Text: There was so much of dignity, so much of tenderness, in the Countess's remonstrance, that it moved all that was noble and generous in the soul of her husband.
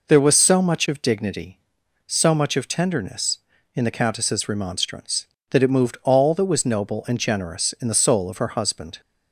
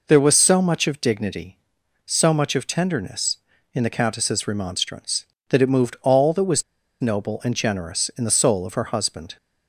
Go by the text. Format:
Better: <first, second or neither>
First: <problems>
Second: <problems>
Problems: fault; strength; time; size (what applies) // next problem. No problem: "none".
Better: first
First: none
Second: pauses between "was" and "noble"; at 6.6 s; 0.37 s long